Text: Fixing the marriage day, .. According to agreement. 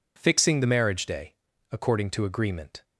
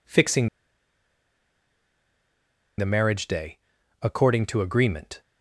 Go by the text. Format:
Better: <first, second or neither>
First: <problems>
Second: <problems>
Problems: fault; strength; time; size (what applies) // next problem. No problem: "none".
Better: first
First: none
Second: pauses between "Fixing" and "the"; strong; at 0.4 s; 2.3 s long